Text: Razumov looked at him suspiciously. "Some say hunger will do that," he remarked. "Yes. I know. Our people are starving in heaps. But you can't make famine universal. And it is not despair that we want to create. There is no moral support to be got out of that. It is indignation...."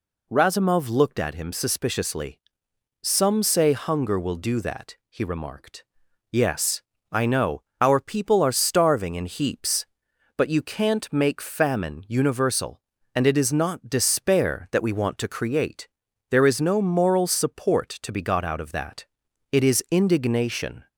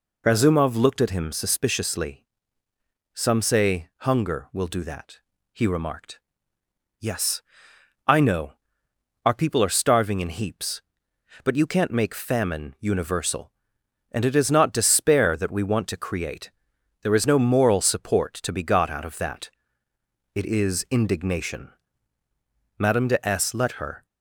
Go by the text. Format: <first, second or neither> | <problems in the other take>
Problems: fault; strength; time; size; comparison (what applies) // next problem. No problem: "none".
first | goes on to say "Madame de S let her"; noticeable; from 22.7 s on; 1.2 s long